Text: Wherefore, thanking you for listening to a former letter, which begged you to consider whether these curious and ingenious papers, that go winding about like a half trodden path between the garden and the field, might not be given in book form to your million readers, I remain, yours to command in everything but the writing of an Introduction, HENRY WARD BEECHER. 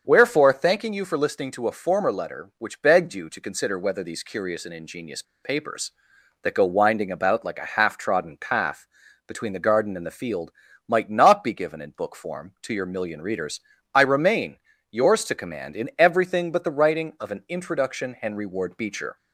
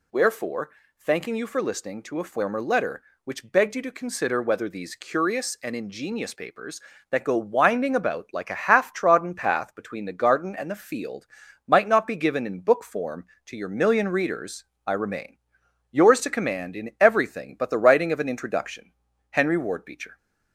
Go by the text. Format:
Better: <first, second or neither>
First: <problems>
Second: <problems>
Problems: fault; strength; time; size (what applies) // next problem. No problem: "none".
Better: second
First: starts louder than the rest; until 1.0 s; 6.5 dB // pauses between "ingenious" and "papers"; slight; at 5.2 s; 0.20 s long // pauses between "path" and "between"; at 8.8 s; 0.40 s long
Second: none